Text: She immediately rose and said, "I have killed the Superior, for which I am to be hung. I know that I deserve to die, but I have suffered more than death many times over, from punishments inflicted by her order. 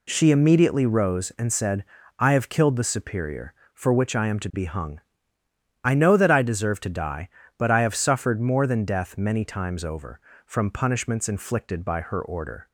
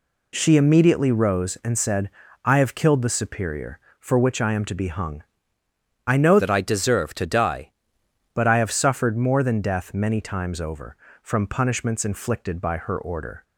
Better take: first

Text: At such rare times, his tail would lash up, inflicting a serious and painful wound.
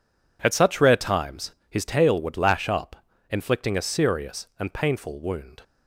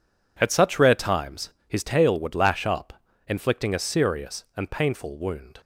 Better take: neither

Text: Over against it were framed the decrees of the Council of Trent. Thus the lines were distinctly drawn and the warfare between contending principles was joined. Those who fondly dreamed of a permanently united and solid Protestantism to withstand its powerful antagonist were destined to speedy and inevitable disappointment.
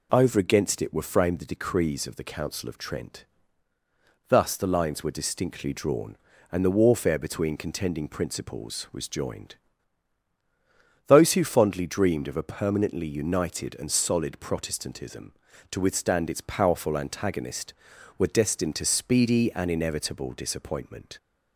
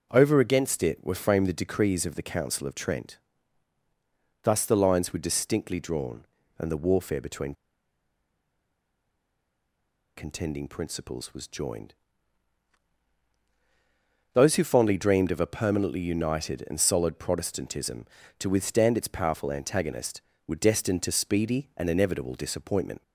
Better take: first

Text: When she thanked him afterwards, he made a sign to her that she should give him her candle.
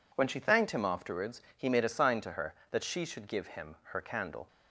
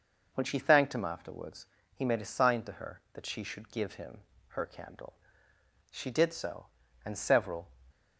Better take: first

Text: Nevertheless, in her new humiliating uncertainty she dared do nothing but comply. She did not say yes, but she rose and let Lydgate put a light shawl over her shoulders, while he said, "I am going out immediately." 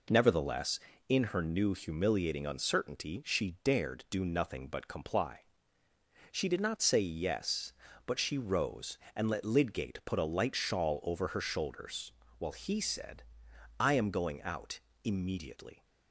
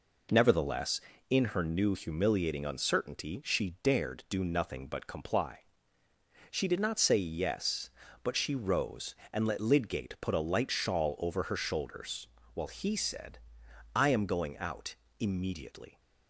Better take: neither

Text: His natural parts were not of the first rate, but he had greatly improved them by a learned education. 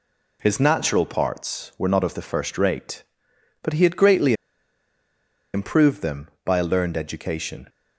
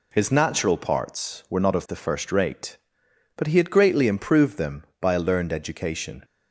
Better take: second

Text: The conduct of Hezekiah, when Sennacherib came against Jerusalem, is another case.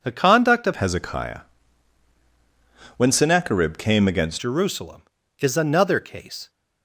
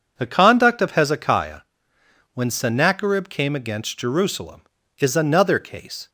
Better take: second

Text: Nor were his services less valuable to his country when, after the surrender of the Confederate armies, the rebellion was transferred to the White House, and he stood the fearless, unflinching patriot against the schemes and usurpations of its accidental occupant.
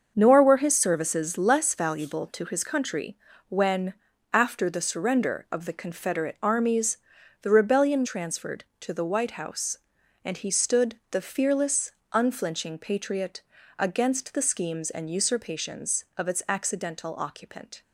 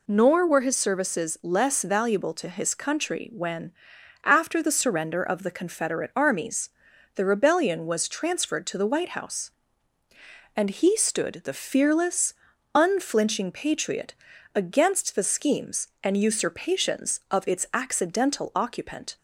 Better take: second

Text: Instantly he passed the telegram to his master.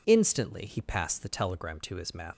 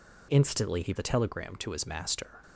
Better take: first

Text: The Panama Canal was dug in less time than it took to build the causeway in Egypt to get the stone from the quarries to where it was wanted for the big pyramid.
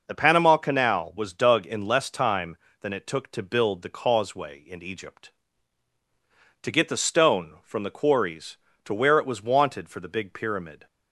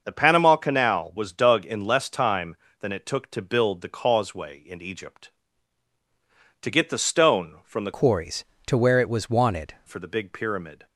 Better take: first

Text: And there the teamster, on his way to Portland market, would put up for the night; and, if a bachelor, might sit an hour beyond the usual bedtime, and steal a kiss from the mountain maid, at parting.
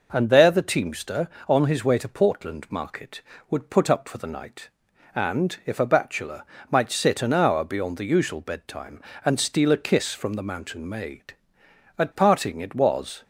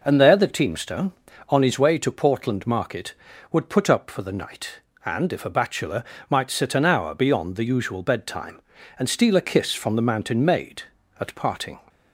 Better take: second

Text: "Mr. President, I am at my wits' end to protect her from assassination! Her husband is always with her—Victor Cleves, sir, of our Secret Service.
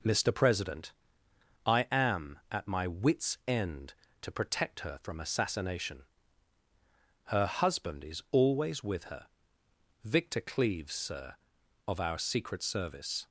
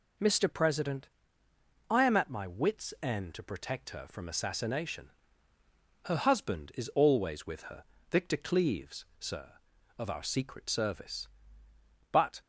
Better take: first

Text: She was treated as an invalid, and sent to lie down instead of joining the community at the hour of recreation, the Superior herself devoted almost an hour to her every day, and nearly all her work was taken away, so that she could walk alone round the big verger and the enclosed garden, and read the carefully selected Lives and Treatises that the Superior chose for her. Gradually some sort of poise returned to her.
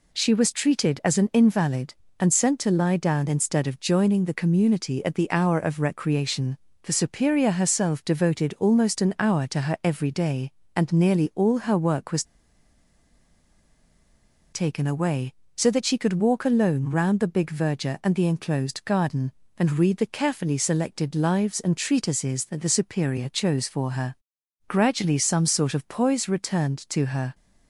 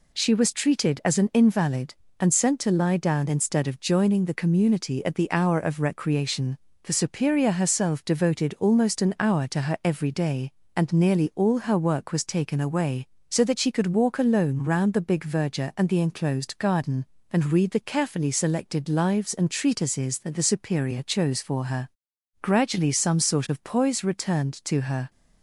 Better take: second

